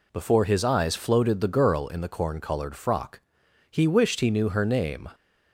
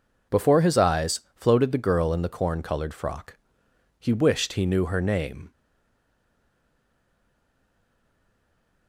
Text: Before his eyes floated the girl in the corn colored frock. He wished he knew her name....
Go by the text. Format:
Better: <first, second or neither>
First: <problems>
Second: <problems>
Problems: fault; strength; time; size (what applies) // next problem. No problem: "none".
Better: first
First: none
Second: stays silent after the last word; strong; from 5.5 s on; 3.3 s long